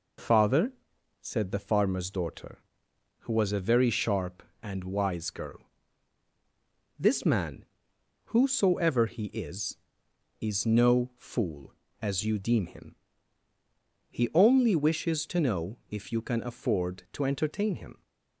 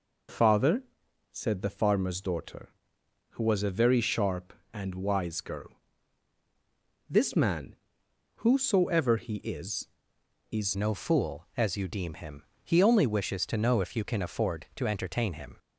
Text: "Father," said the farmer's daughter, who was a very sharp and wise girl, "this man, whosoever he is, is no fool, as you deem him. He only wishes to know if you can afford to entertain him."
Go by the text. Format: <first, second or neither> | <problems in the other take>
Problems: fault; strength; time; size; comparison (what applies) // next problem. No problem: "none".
first | changes voice at "no"; from 10.7 s on; 4.8 s long